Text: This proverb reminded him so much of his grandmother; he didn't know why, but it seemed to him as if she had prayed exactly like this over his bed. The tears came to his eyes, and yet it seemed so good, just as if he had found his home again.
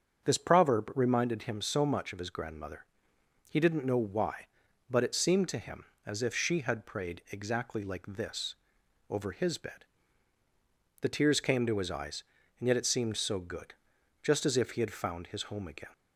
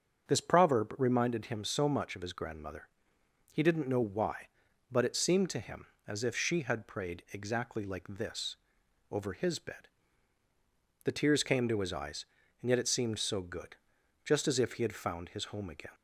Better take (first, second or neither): neither